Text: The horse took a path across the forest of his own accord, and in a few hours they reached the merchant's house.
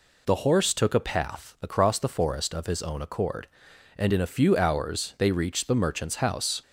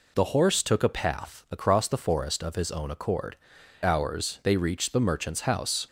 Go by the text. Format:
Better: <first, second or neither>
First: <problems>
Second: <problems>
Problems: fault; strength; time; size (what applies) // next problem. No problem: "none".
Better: first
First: none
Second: skips "and in a few"; at 3.5 s